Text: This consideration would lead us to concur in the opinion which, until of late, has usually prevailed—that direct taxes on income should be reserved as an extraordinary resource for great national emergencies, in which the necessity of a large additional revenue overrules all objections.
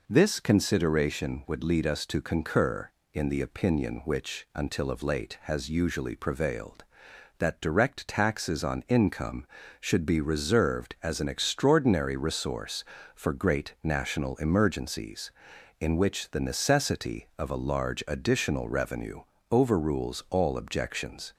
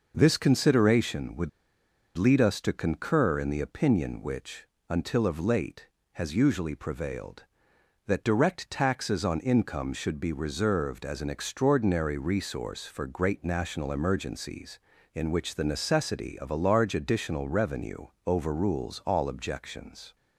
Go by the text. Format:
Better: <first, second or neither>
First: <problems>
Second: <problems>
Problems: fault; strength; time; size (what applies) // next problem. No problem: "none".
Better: first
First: pauses between "revenue" and "overrules"; slight; at 19.2 s; 0.28 s long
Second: pauses between "would" and "lead"; noticeable; at 1.4 s; 0.67 s long // pauses between "revenue" and "overrules"; slight; at 18.0 s; 0.18 s long